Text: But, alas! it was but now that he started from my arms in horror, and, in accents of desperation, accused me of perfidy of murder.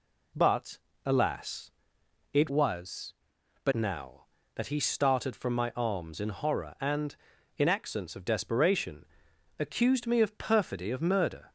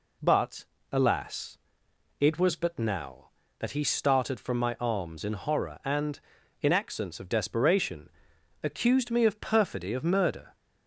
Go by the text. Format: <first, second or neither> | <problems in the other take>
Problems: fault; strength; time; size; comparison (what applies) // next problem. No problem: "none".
second | changes voice from "was" to "but"; from 2.4 to 3.7 s; 1.3 s long